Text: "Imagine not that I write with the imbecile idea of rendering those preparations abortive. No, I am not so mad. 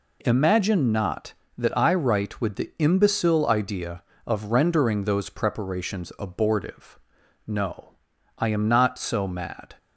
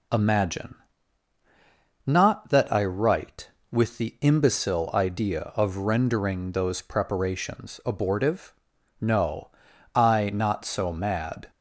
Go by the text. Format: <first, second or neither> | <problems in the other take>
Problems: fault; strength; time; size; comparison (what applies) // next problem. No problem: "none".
first | pauses between "Imagine" and "not"; strong; at 0.7 s; 1.3 s long // skips "am"; at 10.3 s